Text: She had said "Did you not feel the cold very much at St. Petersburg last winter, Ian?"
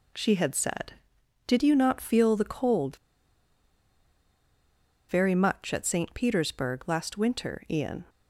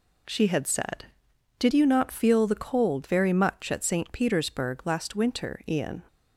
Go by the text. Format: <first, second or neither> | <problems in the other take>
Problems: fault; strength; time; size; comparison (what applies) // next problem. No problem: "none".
second | pauses between "cold" and "very"; strong; at 2.9 s; 2.1 s long